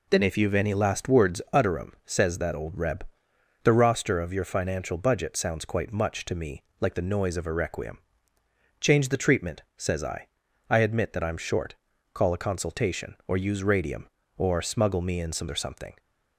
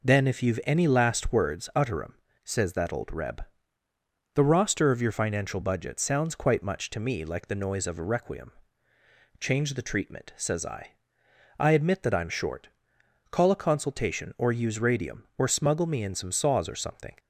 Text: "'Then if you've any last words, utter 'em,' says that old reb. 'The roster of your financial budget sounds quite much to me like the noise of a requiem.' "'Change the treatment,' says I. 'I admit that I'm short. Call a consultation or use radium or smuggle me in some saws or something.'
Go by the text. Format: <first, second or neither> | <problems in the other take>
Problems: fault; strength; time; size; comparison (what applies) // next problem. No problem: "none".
second | pauses between "me" and "like"; slight; at 6.6 s; 0.18 s long // skips "saws"; at 15.4 s